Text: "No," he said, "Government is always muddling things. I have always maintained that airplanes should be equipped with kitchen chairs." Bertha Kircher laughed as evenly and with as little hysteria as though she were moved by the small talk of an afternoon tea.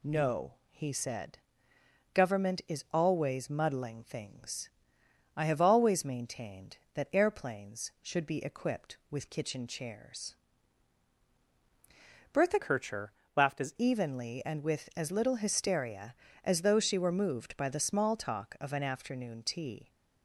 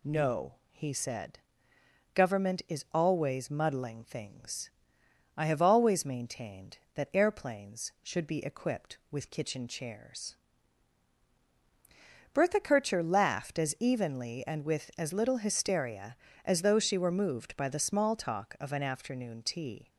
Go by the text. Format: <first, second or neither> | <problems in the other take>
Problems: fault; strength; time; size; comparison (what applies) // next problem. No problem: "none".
second | changes voice from "Kircher" to "as"; from 12.6 to 13.7 s; 1.1 s long // pauses between "Kircher" and "laughed"; slight; at 13.1 s; 0.24 s long